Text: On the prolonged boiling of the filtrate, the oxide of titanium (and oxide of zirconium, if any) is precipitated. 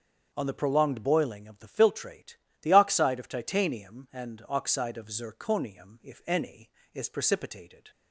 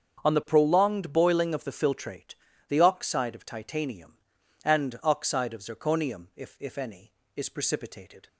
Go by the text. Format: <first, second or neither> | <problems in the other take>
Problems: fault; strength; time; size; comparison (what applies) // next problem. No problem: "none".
first | starts louder than the rest; strong; until 1.3 s; 7.5 dB; also in the first // says "if" twice; at 6.5 s